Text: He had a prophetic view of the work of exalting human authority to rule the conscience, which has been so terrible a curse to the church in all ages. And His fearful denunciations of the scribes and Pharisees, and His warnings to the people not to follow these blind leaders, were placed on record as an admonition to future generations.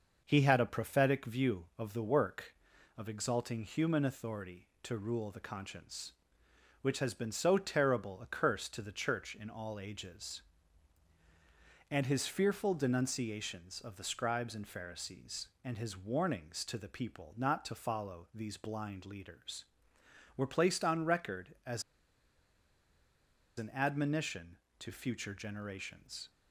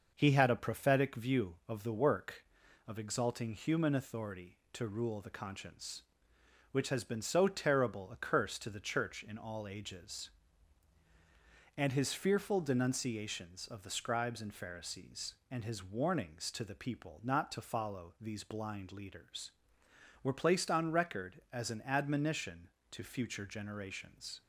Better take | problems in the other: second | starts louder than the rest; noticeable; until 1.2 s; 6 dB; noticeable in the second // pauses between "as" and "an"; strong; at 21.8 s; 1.7 s long

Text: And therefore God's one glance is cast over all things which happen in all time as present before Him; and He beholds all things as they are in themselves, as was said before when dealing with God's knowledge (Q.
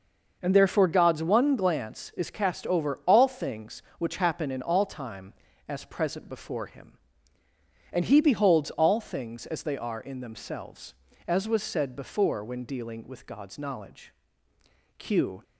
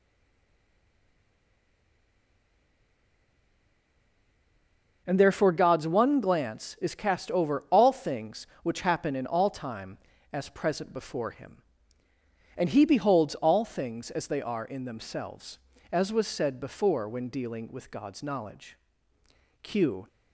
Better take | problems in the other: first | stays silent before the first word; strong; until 5.0 s; 5.0 s long // starts louder than the rest; noticeable; until 6.0 s; 6 dB; noticeable in the first

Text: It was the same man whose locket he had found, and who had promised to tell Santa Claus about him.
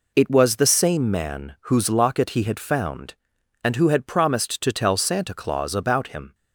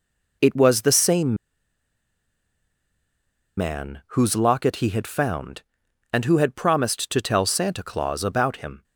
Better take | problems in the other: first | pauses between "same" and "man"; strong; at 1.3 s; 2.2 s long // pauses between "man" and "whose"; slight; at 4.0 s; 0.16 s long; slight in the first

